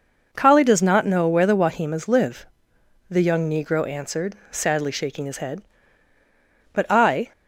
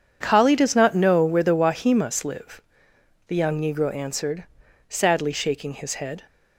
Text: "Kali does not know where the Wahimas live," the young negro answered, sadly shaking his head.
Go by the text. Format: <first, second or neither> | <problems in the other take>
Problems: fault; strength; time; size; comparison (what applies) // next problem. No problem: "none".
second | goes on to say "But I"; from 6.7 s on; 0.60 s long